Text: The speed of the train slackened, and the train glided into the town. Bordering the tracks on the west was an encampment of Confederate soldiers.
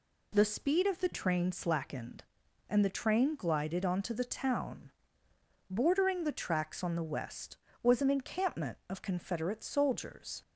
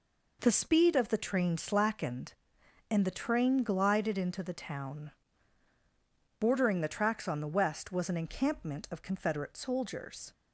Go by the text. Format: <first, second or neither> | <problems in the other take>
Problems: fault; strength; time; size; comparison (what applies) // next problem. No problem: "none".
second | says "onto" for "into"; at 3.8 s